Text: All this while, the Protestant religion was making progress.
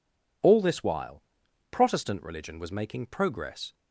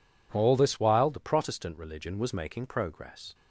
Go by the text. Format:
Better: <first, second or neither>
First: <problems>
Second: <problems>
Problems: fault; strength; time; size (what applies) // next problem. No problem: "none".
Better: second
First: skips "the"; at 1.4 s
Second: none